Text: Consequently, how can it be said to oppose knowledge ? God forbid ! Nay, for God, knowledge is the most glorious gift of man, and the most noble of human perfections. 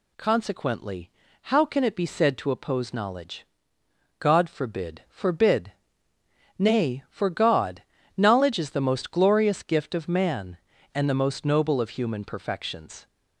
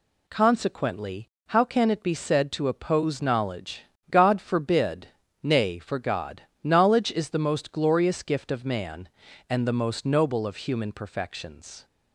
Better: second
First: says "forbid" twice; at 5.0 s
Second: none

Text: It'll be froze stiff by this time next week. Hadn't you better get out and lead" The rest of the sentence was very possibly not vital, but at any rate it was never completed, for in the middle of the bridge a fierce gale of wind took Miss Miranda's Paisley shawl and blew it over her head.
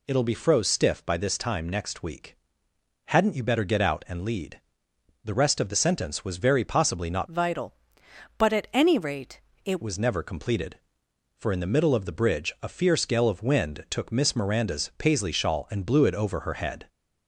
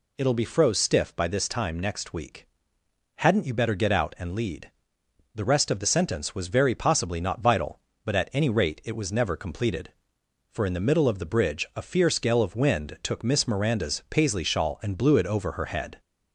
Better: second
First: pauses between "lead" and "The"; noticeable; at 4.5 s; 0.64 s long // changes voice from "vital" to "it"; from 7.2 to 9.8 s; 2.6 s long // pauses between "rate" and "it"; slight; at 9.4 s; 0.26 s long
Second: pauses between "lead" and "The"; noticeable; at 4.6 s; 0.64 s long

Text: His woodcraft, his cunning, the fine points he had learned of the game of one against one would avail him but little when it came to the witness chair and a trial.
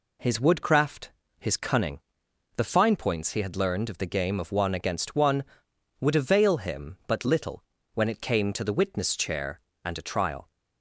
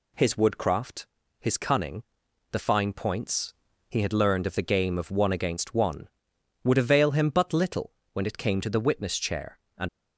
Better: first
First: pauses between "little" and "when"; slight; at 7.6 s; 0.32 s long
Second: pauses between "points" and "he"; slight; at 3.5 s; 0.36 s long // pauses between "little" and "when"; slight; at 7.9 s; 0.22 s long // stops before "a trial"; at 9.8 s

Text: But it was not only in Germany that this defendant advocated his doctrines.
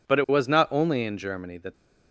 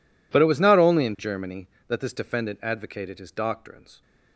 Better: second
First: stops before "this defendant advocated his doctrines"; at 1.7 s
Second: none

